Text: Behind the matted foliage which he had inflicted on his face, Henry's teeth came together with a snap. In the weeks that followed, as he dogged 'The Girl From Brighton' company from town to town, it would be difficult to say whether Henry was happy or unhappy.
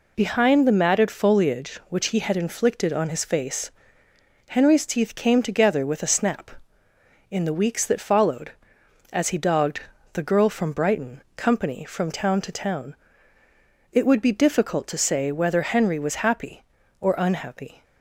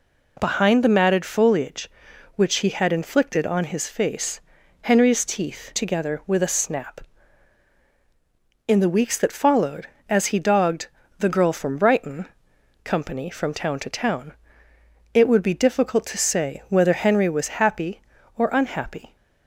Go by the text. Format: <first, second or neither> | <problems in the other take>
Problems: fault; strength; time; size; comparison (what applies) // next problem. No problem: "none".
first | skips "came"; at 5.7 s // pauses between "dogged" and "The"; slight; at 10.8 s; 0.32 s long; slight in the first // pauses between "Brighton" and "company"; noticeable; at 12.2 s; 0.56 s long; slight in the first